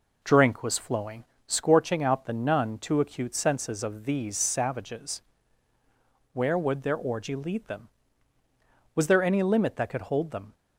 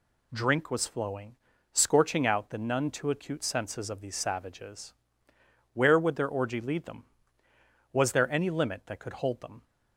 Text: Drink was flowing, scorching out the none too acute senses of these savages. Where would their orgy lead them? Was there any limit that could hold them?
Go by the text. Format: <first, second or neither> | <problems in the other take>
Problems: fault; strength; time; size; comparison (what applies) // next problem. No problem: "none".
second | starts louder than the rest; noticeable; until 1.7 s; 4.5 dB